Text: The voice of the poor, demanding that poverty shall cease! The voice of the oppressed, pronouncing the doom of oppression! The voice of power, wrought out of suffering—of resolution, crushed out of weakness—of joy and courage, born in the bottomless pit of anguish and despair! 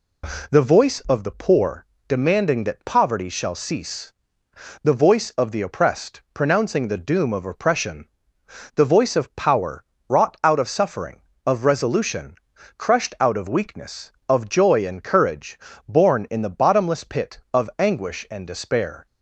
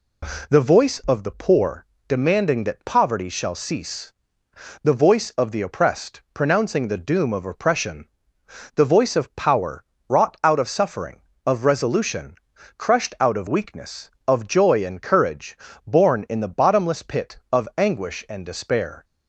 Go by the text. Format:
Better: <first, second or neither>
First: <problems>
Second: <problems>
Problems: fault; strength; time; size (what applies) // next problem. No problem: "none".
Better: neither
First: none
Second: none